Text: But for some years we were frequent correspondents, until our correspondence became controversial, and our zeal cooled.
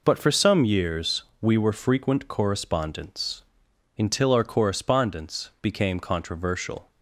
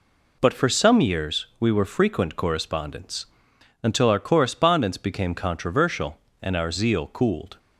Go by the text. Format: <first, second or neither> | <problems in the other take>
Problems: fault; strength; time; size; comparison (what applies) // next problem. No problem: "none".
second | pauses between "years" and "we"; slight; at 1.2 s; 0.16 s long // stops before "and our zeal cooled"; at 6.9 s